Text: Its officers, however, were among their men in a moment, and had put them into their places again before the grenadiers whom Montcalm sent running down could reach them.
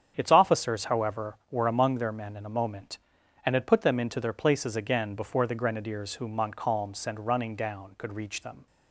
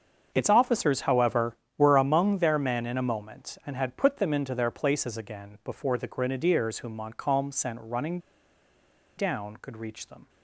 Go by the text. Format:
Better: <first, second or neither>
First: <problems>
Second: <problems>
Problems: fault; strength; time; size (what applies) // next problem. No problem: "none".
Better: first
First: starts louder than the rest; strong; until 1.1 s; 8.5 dB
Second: starts louder than the rest; until 1.3 s; 7 dB // pauses between "running" and "down"; at 8.1 s; 0.99 s long